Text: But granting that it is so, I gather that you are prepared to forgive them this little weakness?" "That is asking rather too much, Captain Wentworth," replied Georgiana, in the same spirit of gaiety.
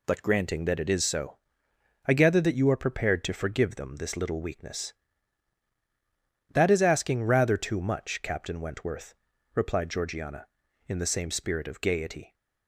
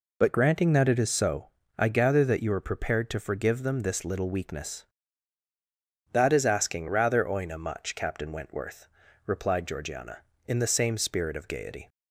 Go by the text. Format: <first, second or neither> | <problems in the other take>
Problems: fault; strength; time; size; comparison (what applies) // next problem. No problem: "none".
first | says "oina" for "too"; at 7.2 s